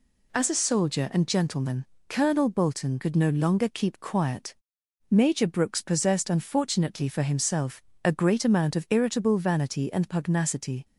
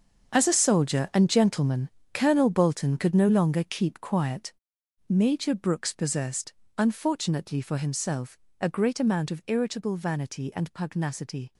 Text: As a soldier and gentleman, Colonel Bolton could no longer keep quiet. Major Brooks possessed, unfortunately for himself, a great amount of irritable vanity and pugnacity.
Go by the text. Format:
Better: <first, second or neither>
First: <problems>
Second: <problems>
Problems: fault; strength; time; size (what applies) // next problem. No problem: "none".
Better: first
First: none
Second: gets quieter; strong; throughout; 13 dB